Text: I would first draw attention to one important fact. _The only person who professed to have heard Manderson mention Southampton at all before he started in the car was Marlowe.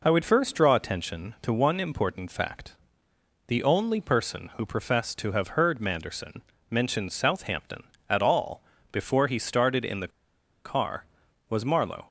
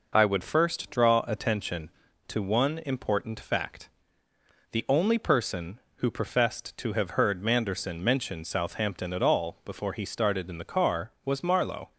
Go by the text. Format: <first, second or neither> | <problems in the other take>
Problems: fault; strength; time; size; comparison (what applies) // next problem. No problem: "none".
second | pauses between "Manderson" and "mention"; slight; at 6.4 s; 0.28 s long // pauses between "all" and "before"; slight; at 8.6 s; 0.30 s long // pauses between "the" and "car"; noticeable; at 10.1 s; 0.56 s long